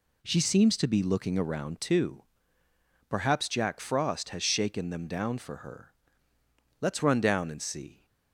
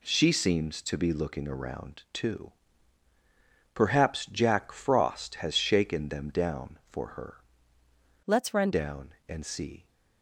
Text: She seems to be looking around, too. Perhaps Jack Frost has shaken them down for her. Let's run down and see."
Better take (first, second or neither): first